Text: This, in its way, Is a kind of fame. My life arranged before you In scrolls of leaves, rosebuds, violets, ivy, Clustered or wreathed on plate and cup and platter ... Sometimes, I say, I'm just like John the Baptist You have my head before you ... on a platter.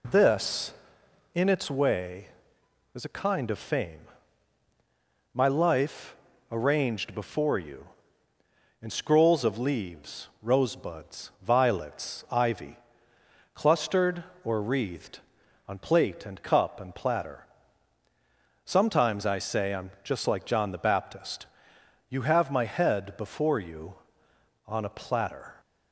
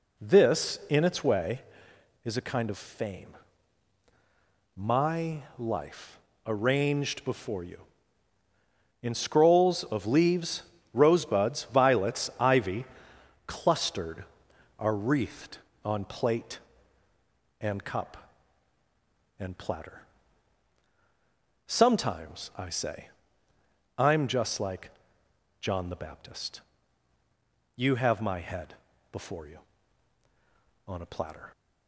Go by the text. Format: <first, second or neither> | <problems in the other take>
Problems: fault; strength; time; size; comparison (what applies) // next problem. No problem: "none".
first | pauses between "life" and "arranged"; slight; at 6.1 s; 0.26 s long; slight in the first // says "are" for "or"; at 14.7 s // pauses between "like" and "John"; noticeable; at 24.8 s; 0.70 s long // pauses between "Baptist" and "You"; at 26.6 s; 1.1 s long; noticeable in the first // pauses between "head" and "before"; at 28.7 s; 0.38 s long